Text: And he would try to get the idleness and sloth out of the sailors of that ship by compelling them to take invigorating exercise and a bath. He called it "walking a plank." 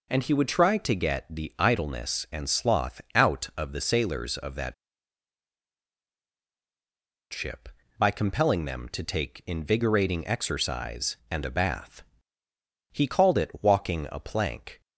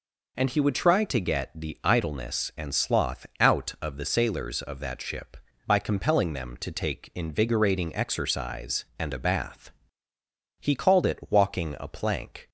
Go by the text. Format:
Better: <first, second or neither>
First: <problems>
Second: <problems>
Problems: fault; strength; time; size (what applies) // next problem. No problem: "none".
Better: second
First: pauses between "that" and "ship"; strong; at 4.7 s; 2.5 s long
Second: none